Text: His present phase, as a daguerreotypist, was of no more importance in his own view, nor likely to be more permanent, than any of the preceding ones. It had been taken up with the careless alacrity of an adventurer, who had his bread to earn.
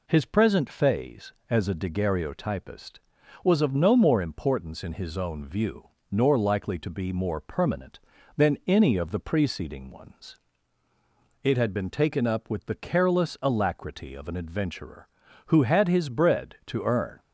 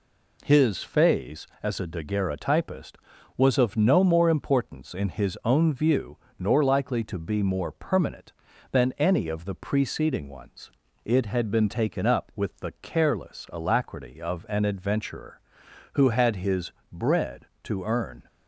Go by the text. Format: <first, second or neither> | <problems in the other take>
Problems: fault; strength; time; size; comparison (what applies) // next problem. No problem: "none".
first | skips "present"; at 0.8 s // pauses between "his" and "bread"; slight; at 16.7 s; 0.22 s long